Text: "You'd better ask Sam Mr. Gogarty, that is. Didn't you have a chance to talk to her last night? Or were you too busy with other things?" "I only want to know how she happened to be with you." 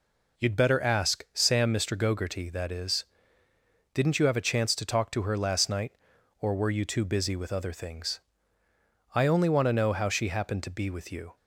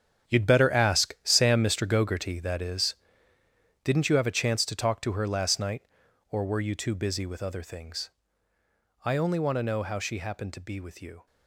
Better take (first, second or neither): first